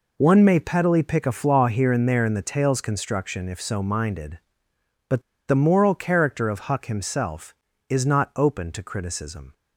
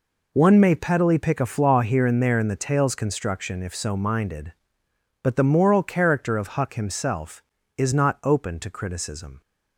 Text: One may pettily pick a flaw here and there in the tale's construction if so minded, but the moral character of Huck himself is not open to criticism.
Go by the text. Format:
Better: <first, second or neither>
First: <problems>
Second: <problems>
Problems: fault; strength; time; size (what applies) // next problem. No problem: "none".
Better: second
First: pauses between "but" and "the"; slight; at 5.2 s; 0.26 s long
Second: none